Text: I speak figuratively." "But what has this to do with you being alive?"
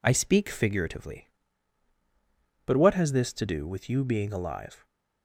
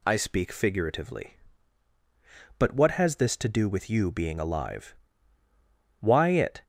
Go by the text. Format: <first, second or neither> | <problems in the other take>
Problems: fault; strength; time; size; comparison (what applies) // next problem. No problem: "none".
first | goes on to say "Why it"; noticeable; from 5.9 s on; 0.64 s long